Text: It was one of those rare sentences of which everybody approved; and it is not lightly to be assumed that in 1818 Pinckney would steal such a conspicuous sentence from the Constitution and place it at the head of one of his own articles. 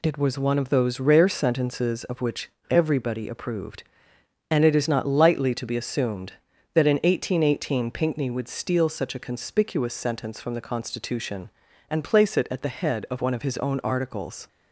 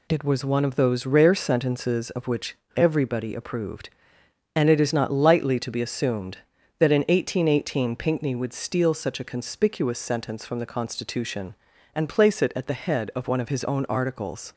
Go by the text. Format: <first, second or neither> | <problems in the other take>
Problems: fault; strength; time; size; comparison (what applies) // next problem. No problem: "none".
neither | pauses between "which" and "everybody"; slight; the same in both